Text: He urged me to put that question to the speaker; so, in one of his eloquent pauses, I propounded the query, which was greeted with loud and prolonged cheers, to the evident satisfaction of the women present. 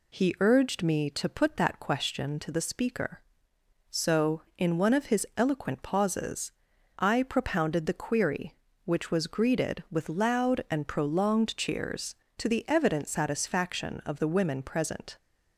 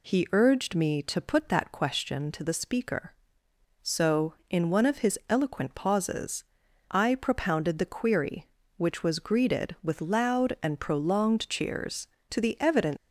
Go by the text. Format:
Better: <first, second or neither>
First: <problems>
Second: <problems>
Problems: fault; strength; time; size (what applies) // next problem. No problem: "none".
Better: first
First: none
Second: stops before "satisfaction of the women present"; at 12.9 s